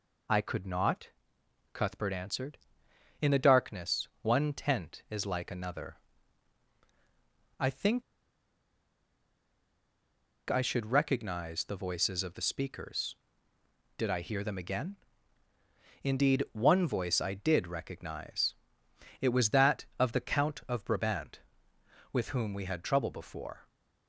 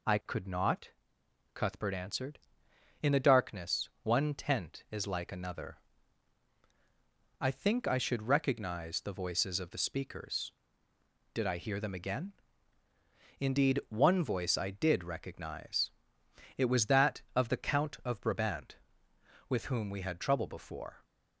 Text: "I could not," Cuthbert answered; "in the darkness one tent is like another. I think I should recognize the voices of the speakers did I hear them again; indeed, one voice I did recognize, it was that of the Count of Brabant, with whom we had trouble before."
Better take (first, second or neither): second